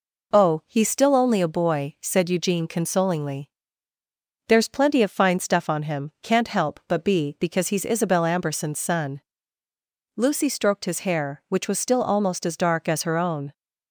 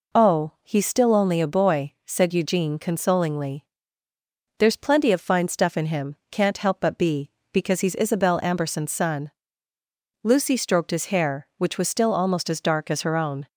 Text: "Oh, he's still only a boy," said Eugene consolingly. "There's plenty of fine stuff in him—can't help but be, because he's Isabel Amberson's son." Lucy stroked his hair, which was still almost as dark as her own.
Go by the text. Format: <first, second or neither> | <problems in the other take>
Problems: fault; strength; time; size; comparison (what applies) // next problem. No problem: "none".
second | says "on" for "in"; at 5.6 s